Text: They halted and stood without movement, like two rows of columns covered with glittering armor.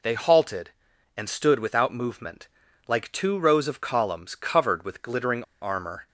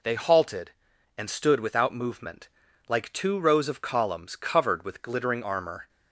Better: second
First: pauses between "glittering" and "armor"; slight; at 5.4 s; 0.19 s long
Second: none

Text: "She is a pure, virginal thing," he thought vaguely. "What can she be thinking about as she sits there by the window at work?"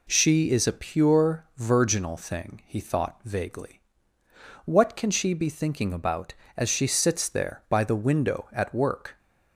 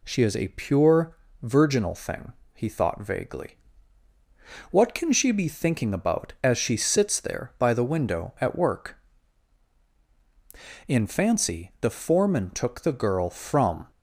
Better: first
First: none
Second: goes on to say "In fancy the foreman took the girl from"; strong; from 10.8 s on; 2.9 s long

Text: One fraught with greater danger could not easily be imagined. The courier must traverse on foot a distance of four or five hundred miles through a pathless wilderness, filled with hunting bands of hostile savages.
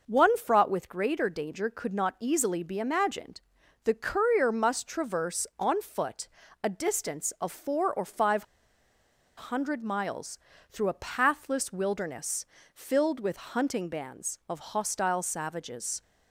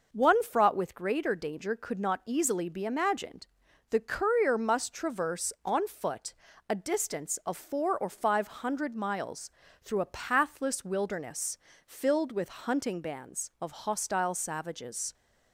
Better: second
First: pauses between "foot" and "a"; slight; at 6.2 s; 0.36 s long // pauses between "five" and "hundred"; noticeable; at 8.4 s; 0.94 s long // pauses between "miles" and "through"; slight; at 10.3 s; 0.32 s long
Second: pauses between "foot" and "a"; slight; at 6.3 s; 0.36 s long // pauses between "miles" and "through"; slight; at 9.5 s; 0.32 s long

